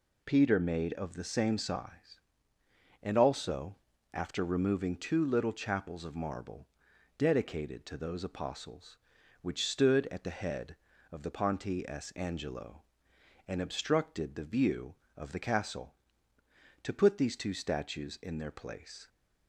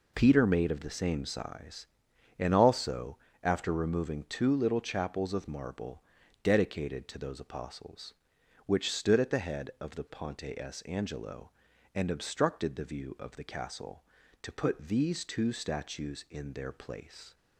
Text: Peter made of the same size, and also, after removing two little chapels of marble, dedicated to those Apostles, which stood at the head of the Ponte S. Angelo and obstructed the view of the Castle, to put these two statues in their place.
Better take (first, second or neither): neither